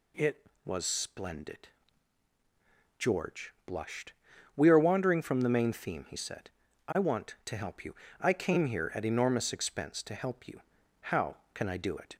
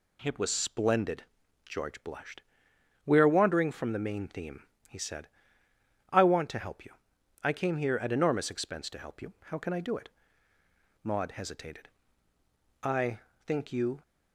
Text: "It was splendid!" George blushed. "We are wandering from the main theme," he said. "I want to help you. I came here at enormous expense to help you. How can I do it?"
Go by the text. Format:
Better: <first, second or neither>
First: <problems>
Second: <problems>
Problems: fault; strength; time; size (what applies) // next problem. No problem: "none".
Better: first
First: none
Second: goes on to say "Maud hesitated I think you"; strong; from 11.0 s on; 2.9 s long